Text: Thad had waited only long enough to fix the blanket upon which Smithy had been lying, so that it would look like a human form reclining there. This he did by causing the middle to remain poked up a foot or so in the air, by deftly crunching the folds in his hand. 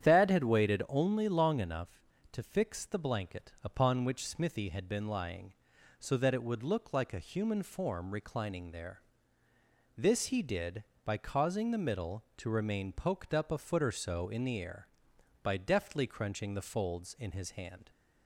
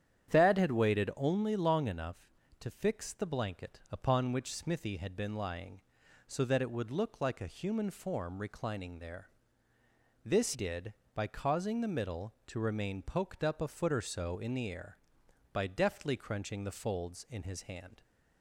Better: first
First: starts louder than the rest; strong; until 1.1 s; 9.5 dB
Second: starts louder than the rest; strong; until 1.3 s; 9.5 dB // skips "he"; at 10.5 s

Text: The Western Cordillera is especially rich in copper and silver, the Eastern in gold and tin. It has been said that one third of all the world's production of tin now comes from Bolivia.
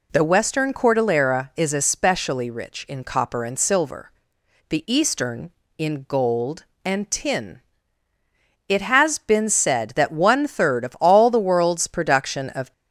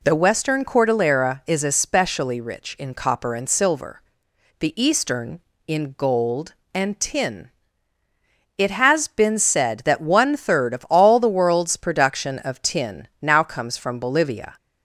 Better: second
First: stops before "tin now comes from Bolivia"; at 12.7 s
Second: none

